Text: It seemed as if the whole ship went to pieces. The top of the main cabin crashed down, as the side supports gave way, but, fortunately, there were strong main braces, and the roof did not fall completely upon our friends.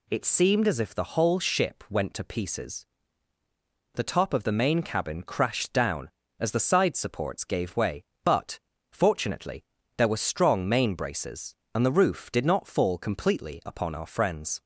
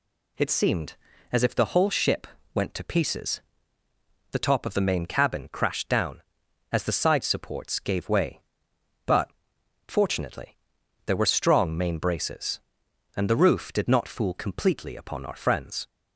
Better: first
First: none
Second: pauses between "ship" and "went"; slight; at 2.2 s; 0.26 s long // says "fool" for "fall"; at 14.0 s

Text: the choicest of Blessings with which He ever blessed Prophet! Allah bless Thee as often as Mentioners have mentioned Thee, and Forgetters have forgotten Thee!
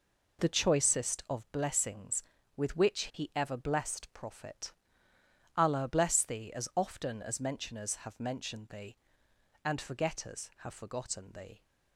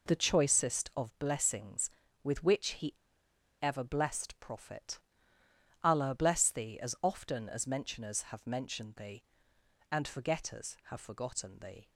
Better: first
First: none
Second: pauses between "He" and "ever"; noticeable; at 2.9 s; 0.67 s long

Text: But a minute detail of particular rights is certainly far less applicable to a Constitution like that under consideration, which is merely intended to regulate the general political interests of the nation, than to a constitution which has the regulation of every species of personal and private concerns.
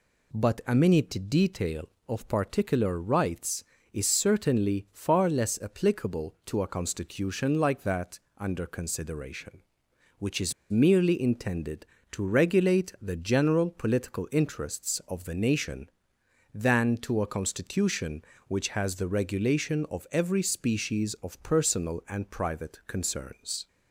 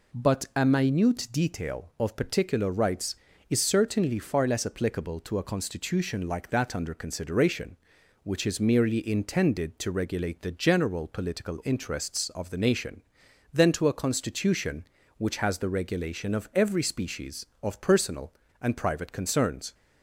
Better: second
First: pauses between "that" and "under"; slight; at 8.1 s; 0.20 s long // pauses between "is" and "merely"; slight; at 10.5 s; 0.17 s long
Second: none

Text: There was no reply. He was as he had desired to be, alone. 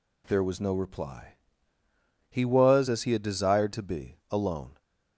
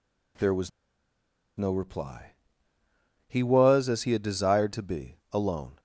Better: first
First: none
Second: pauses between "was" and "no"; noticeable; at 0.6 s; 0.87 s long

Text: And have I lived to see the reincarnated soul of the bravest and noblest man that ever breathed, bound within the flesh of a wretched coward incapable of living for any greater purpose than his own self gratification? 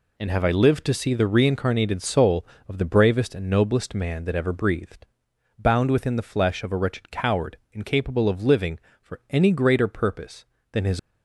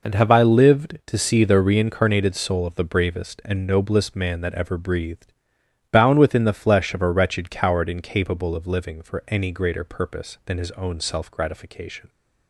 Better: second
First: pauses between "coward" and "incapable"; slight; at 7.5 s; 0.16 s long // stops before "own self gratification"; at 10.9 s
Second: none

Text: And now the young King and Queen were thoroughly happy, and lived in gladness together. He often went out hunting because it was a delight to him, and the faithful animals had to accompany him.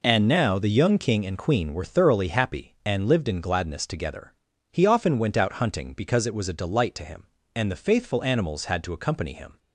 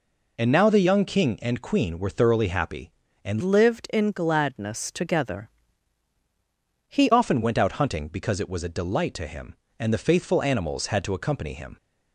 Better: first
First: none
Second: changes voice from "lived" to "He"; from 3.4 to 7.0 s; 3.6 s long

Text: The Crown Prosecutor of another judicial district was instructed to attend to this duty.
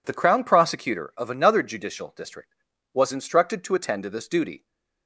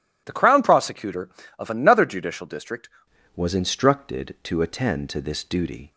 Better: first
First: none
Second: changes voice at "was"; from 3.3 s on; 2.6 s long

